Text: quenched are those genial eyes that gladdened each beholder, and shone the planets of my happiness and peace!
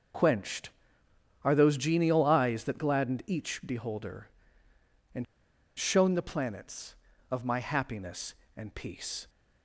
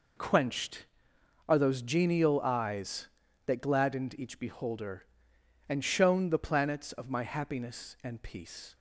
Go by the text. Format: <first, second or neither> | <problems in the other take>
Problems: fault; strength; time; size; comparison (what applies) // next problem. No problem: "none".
second | pauses between "and" and "shone"; noticeable; at 5.2 s; 0.54 s long